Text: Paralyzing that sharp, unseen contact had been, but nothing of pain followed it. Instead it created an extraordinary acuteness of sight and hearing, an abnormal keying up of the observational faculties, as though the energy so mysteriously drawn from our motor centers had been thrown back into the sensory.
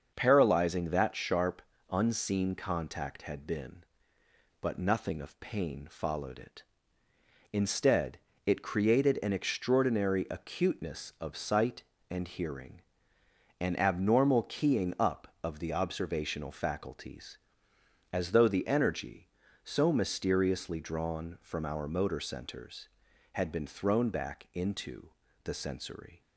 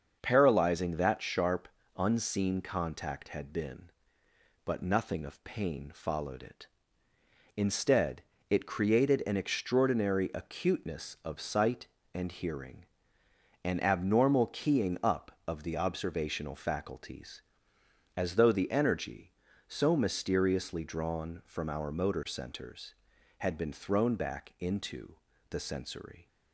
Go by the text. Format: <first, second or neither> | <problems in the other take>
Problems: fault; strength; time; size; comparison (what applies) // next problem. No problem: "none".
neither | starts louder than the rest; the same in both // pauses between "Instead" and "it"; slight; the same in both // pauses between "into" and "the"; slight; the same in both